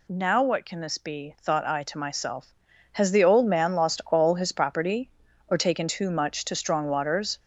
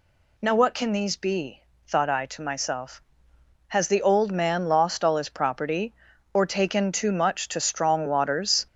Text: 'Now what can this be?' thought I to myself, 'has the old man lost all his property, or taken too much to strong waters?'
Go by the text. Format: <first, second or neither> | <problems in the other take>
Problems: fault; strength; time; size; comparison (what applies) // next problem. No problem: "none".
first | says "these" for "this"; at 0.9 s